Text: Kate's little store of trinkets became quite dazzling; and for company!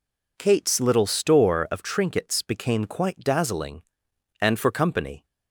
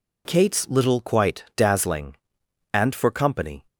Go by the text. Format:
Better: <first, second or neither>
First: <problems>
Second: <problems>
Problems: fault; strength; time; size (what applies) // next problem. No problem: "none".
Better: first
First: none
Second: skips "store of trinkets became"; at 1.0 s